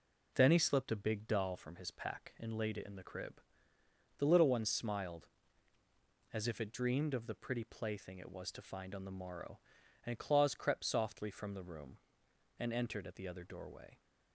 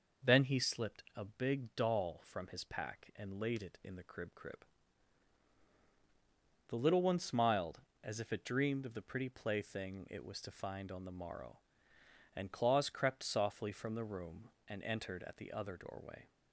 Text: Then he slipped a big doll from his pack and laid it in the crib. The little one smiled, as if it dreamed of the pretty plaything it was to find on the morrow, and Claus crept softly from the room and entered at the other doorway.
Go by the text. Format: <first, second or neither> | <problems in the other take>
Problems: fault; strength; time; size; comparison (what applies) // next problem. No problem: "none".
first | says "crib" twice; at 4.3 s